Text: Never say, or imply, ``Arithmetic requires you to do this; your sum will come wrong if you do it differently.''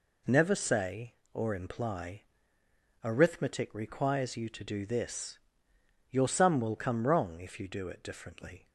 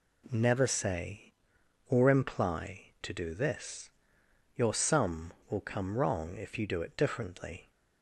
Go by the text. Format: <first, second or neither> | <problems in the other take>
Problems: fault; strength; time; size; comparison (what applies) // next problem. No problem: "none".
first | skips "Arithmetic requires you"; at 2.9 s